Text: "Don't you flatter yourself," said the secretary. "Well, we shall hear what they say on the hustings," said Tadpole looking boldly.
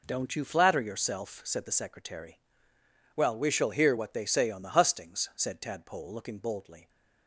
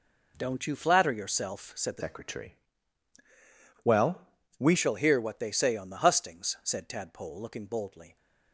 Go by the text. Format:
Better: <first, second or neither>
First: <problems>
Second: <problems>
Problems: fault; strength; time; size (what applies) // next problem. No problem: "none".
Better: first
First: none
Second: changes voice from "secretary" to "we"; from 1.9 to 4.7 s; 2.8 s long